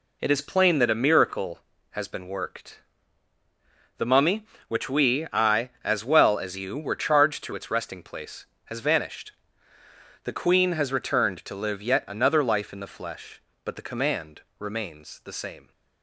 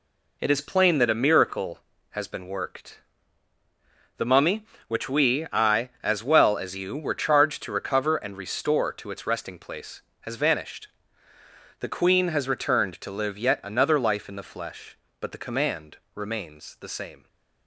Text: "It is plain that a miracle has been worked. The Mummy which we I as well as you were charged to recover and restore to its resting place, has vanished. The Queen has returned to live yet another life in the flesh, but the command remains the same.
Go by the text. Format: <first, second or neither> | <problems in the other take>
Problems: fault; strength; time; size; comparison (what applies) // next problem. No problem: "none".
second | skips "recover and restore to"; at 7.5 s // pauses between "command" and "remains"; slight; at 14.4 s; 0.16 s long; slight in the second